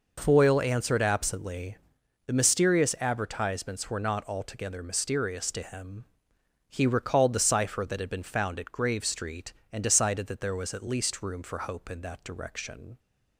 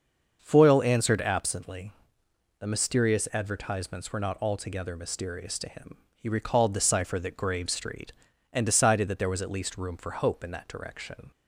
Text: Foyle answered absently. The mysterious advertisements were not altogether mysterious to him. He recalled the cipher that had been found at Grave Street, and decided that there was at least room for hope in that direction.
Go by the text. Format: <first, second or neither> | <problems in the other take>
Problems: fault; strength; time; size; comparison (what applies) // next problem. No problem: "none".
first | starts louder than the rest; until 1.4 s; 6.5 dB // skips "had been found at"; at 7.3 s